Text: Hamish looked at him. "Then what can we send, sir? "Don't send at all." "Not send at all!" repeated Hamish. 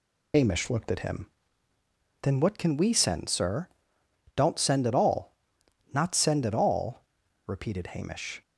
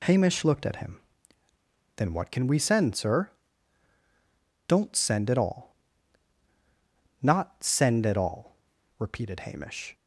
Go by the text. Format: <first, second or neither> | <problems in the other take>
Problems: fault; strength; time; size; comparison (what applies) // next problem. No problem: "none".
second | loses the start of "Hamish"; at 0.3 s; 80 ms